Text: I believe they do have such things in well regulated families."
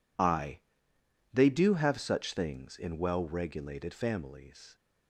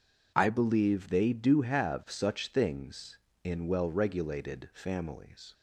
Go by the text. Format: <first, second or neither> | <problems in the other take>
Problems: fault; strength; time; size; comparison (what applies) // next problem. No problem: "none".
second | skips "believe"; at 0.9 s